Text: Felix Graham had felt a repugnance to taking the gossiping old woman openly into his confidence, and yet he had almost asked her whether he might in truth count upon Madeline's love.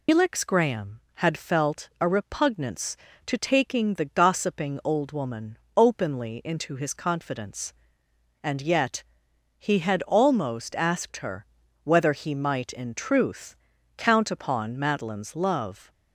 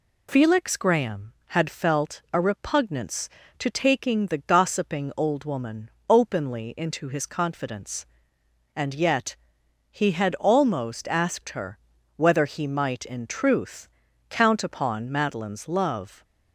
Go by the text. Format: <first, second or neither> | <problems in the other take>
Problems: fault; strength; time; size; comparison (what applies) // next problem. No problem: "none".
second | loses the start of "Felix"; at 0.0 s; 125 ms // pauses between "woman" and "openly"; slight; at 5.5 s; 0.18 s long; slight in the second // pauses between "yet" and "he"; noticeable; at 9.0 s; 0.54 s long; noticeable in the second // pauses between "her" and "whether"; slight; at 11.4 s; 0.36 s long; slight in the second // pauses between "truth" and "count"; at 13.5 s; 0.42 s long; also in the second